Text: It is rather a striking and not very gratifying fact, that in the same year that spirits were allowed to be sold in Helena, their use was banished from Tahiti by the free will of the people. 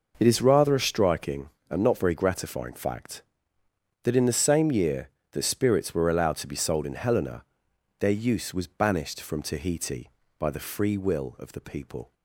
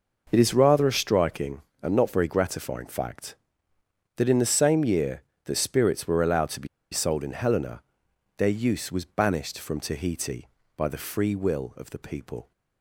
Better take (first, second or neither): first